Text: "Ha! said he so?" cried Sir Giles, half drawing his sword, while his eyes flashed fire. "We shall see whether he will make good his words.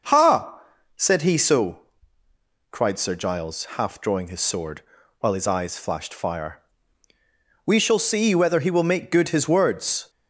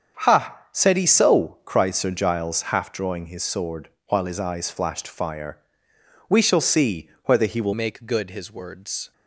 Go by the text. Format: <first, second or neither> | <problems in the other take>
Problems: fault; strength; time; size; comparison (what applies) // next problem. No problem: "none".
first | starts louder than the rest; until 1.2 s; 6.5 dB // pauses between "see" and "whether"; slight; at 7.0 s; 0.16 s long // changes voice at "make"; from 7.7 s on; 1.4 s long